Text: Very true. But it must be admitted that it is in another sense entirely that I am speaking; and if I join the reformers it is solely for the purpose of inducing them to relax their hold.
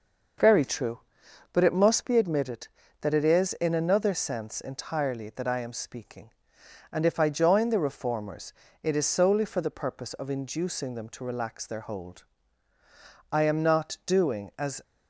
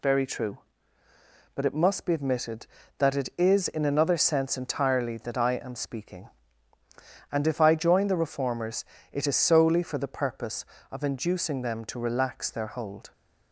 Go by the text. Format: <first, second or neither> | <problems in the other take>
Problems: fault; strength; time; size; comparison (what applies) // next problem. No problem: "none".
second | starts louder than the rest; noticeable; until 1.9 s; 6 dB // pauses between "reformers" and "it"; slight; at 8.5 s; 0.32 s long; slight in the second // goes on to say "I am not doing as"; from 13.3 s on; 1.4 s long